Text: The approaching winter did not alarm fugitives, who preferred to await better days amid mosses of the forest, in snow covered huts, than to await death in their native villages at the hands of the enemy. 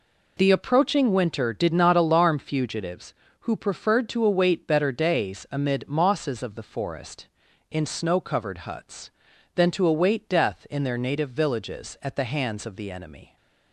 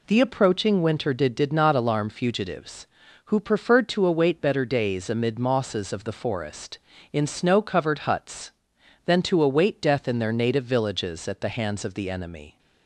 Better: first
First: none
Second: says "did" twice; at 1.3 s

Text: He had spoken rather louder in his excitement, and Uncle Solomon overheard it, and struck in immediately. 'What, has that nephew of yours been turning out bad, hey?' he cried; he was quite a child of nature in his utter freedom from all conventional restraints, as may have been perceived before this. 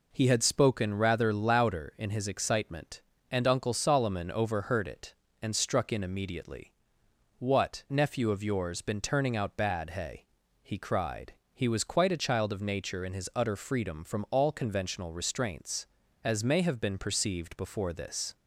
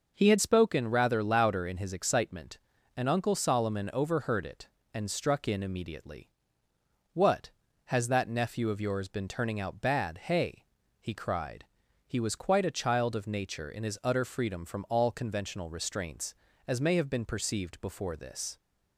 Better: second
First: skips "has that"; at 7.8 s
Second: none

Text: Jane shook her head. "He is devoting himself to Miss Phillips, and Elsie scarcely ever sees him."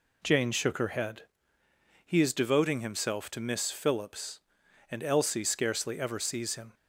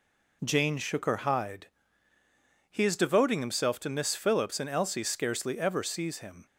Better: first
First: none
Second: says "hide" for "head"; at 1.1 s

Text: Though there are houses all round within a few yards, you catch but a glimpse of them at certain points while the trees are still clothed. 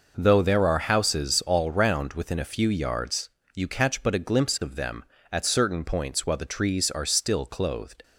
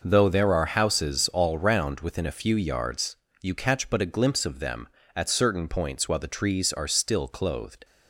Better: neither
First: none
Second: none

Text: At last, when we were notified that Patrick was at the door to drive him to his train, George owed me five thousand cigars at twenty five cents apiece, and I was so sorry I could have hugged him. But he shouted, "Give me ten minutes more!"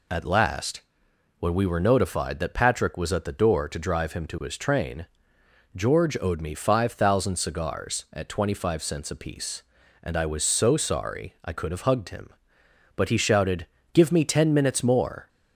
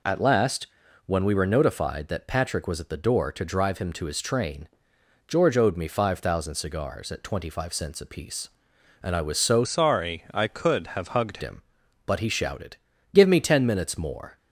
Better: first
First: none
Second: changes voice from "sorry" to "hugged"; from 9.6 to 11.3 s; 1.7 s long

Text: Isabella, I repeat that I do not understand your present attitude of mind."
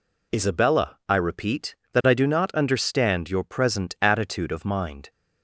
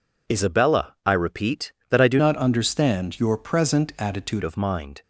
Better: first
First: none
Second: changes voice from "not" to "attitude"; from 2.1 to 4.4 s; 2.3 s long

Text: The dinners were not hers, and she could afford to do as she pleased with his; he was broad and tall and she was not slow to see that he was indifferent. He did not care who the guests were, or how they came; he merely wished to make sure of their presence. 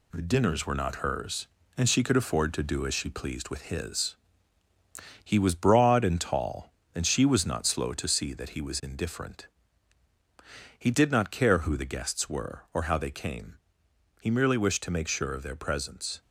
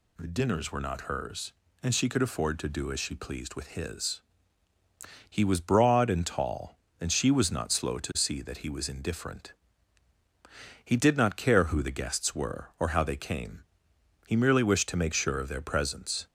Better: second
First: gets quieter; noticeable; throughout; 4 dB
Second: none

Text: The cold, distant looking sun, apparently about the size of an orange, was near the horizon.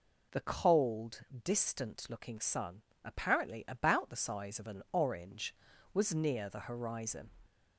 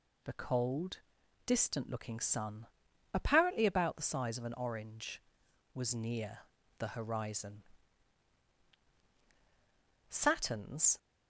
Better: first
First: none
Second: pauses between "near" and "the"; at 6.3 s; 0.38 s long // goes on to say "Saturn's"; noticeable; from 10.0 s on; 0.88 s long

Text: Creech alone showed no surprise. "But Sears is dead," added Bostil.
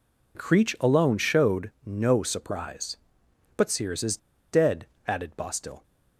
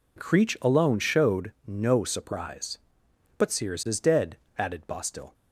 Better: second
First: pauses between "showed" and "no"; slight; at 1.6 s; 0.16 s long // pauses between "is" and "dead"; slight; at 4.1 s; 0.34 s long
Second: pauses between "showed" and "no"; slight; at 1.5 s; 0.16 s long

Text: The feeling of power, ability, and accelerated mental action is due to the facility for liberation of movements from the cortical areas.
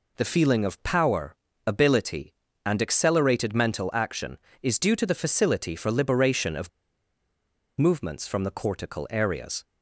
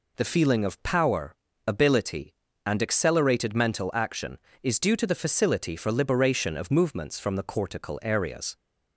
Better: second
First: pauses between "of" and "movements"; at 6.6 s; 1.0 s long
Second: none

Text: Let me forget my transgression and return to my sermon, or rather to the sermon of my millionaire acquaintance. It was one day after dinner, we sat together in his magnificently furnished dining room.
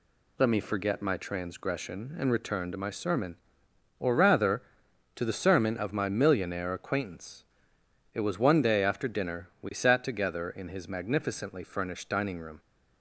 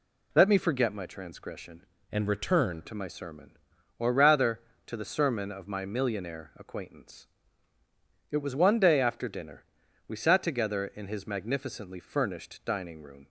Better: first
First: none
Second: changes voice from "and" to "return"; from 2.1 to 2.8 s; 0.7 s long

